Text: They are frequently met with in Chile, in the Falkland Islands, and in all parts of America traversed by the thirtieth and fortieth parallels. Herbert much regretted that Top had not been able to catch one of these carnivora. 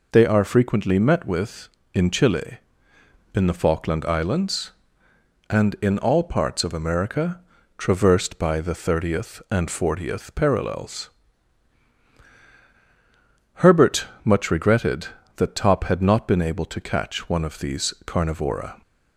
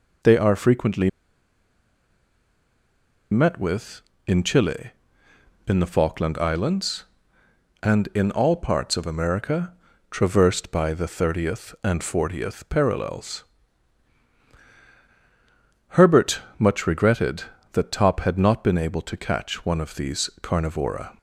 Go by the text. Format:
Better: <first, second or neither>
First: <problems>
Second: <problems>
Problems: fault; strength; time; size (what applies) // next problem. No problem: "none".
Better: first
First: pauses between "America" and "traversed"; slight; at 7.4 s; 0.36 s long // pauses between "Herbert" and "much"; slight; at 14.0 s; 0.18 s long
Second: pauses between "frequently" and "met"; strong; at 1.0 s; 2.2 s long // pauses between "America" and "traversed"; slight; at 9.7 s; 0.36 s long // pauses between "Herbert" and "much"; slight; at 16.3 s; 0.18 s long